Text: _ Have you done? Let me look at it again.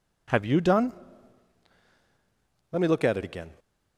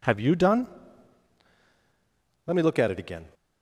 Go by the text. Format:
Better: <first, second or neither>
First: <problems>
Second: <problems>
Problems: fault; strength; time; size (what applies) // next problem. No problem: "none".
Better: neither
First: none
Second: none